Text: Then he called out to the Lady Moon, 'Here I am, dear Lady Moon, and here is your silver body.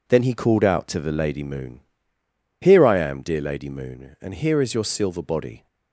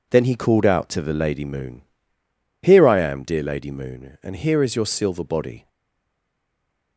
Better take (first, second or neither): first